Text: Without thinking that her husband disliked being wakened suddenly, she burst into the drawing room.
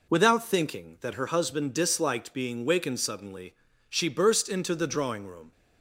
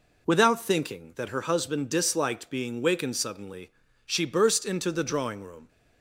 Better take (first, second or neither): neither